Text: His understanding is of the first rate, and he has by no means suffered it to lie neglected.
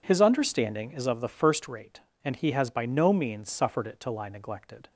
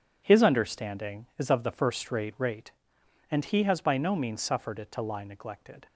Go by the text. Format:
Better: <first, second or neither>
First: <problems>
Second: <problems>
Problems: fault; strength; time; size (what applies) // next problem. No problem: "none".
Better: first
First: none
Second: says "rate" twice; at 2.3 s